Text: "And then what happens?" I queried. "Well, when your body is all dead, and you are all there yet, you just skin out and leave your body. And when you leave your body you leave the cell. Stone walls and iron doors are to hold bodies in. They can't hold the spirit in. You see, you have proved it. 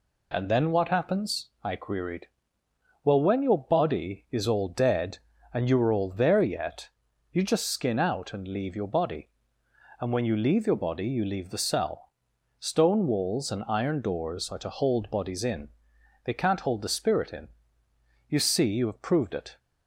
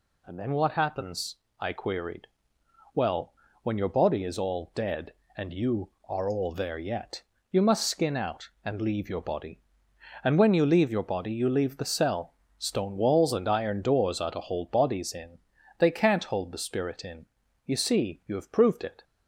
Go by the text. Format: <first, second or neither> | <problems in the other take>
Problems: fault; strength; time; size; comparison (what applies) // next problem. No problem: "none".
first | says "must" for "just"; at 7.6 s